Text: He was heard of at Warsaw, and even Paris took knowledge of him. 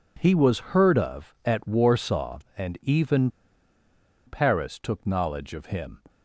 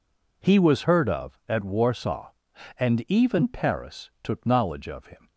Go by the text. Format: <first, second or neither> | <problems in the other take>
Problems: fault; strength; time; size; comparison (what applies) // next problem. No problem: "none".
second | pauses between "even" and "Paris"; noticeable; at 3.2 s; 0.97 s long